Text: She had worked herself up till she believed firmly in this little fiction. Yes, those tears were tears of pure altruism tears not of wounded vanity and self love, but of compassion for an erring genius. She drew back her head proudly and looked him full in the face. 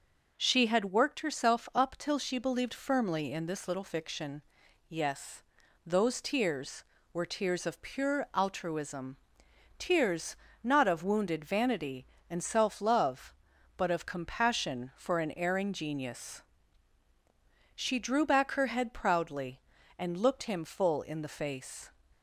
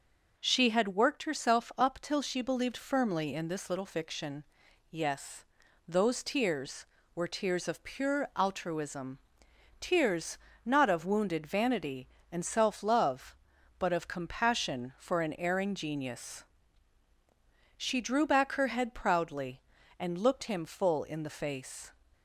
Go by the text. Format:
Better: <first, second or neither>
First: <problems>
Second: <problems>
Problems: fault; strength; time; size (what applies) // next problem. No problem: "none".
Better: neither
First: pauses between "altruism" and "tears"; noticeable; at 9.1 s; 0.60 s long // pauses between "tears" and "not"; slight; at 10.3 s; 0.28 s long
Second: pauses between "altruism" and "tears"; noticeable; at 9.1 s; 0.60 s long // pauses between "tears" and "not"; slight; at 10.3 s; 0.28 s long